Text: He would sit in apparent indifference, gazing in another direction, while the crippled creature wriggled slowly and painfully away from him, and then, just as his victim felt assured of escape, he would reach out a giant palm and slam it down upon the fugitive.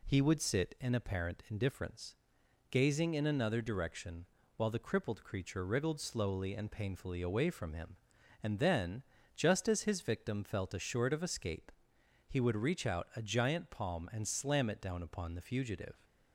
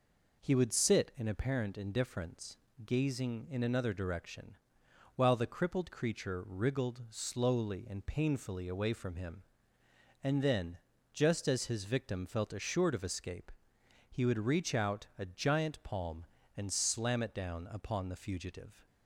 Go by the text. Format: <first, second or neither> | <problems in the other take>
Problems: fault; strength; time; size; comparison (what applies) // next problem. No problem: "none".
neither | none